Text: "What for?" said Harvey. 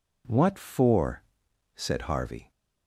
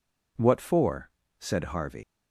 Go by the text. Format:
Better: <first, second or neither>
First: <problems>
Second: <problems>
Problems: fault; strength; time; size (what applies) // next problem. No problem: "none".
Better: first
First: none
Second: leaves "Harvey" unfinished; at 2.0 s; 105 ms